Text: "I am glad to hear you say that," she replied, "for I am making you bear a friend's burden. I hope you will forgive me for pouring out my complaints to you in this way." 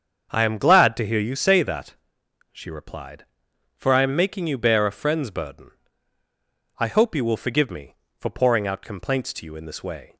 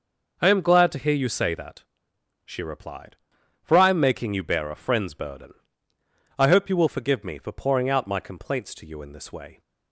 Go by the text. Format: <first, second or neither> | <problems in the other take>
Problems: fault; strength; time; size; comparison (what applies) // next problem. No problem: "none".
second | starts louder than the rest; until 1.3 s; 7 dB // skips "my"; at 8.8 s